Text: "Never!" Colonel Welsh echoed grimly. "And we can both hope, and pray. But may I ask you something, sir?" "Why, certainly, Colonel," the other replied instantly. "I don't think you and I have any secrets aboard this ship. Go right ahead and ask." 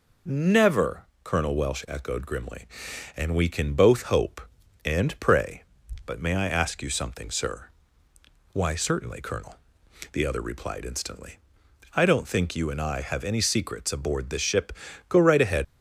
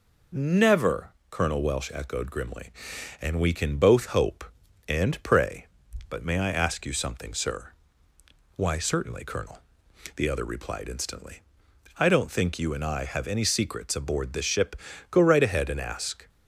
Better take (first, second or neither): second